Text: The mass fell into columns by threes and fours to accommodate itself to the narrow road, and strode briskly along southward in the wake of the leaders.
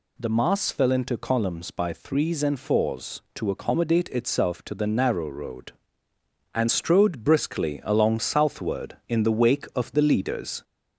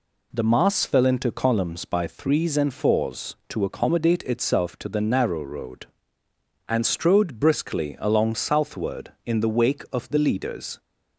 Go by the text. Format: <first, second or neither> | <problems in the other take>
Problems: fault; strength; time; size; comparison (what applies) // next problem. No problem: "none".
second | gets louder; slight; throughout; 2 dB